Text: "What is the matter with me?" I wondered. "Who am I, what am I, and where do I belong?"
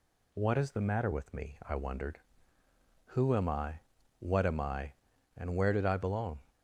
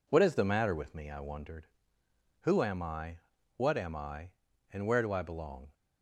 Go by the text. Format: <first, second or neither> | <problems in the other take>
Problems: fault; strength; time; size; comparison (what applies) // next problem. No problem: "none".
second | says "did" for "do"; at 5.7 s